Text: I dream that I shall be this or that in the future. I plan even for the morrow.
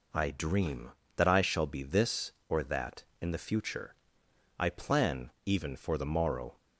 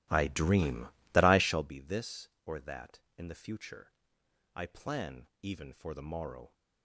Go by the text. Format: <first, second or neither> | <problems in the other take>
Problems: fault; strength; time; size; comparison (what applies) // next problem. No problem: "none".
first | starts louder than the rest; strong; until 1.8 s; 15 dB // pauses between "plan" and "even"; slight; at 5.2 s; 0.16 s long; slight in the first